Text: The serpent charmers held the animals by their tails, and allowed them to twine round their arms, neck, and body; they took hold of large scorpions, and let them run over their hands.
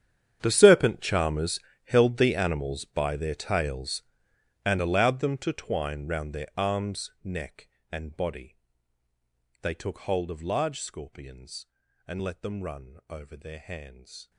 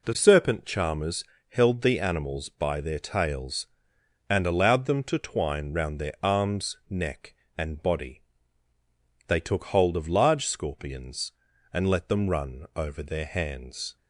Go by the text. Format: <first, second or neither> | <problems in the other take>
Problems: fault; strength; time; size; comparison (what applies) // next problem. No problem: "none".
second | gets quieter; strong; throughout; 18.5 dB // pauses between "charmers" and "held"; slight; at 1.5 s; 0.24 s long; slight in the second